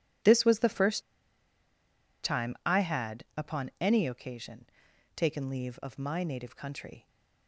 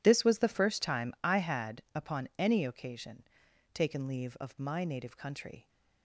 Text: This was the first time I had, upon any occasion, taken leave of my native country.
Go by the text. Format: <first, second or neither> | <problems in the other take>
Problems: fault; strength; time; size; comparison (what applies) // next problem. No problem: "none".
second | pauses between "first" and "time"; at 1.0 s; 1.2 s long